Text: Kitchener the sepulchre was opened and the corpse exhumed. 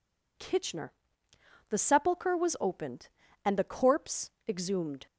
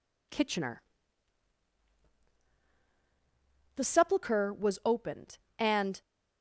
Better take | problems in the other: first | pauses between "Kitchener" and "the"; strong; at 0.8 s; 2.9 s long; noticeable in the first // stops before "the corpse exhumed"; at 6.0 s

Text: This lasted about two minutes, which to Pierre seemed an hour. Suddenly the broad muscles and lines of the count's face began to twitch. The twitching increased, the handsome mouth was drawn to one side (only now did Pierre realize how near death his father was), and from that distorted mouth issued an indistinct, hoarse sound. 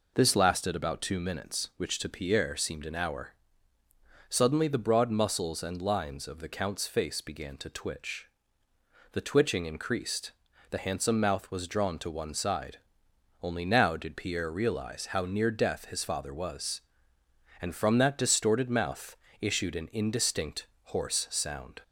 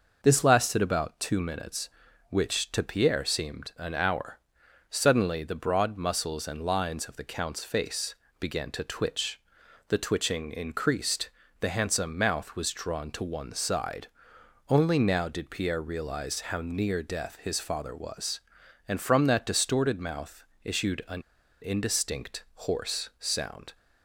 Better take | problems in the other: first | pauses between "face" and "began"; slight; at 8.1 s; 0.24 s long // pauses between "mouth" and "issued"; slight; at 20.4 s; 0.20 s long; slight in the first // pauses between "an" and "indistinct"; at 21.2 s; 0.39 s long

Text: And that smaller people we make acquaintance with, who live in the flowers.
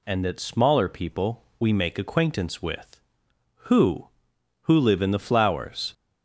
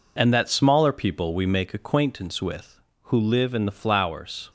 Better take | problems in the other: second | pauses between "people" and "we"; slight; at 1.4 s; 0.16 s long // says "who" twice; at 4.6 s

